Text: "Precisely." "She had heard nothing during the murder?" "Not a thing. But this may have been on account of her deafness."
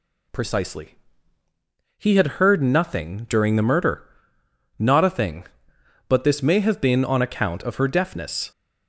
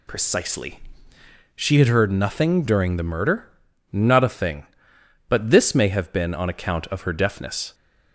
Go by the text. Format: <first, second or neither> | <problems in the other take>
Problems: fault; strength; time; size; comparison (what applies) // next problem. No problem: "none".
second | says "He" for "She"; at 1.9 s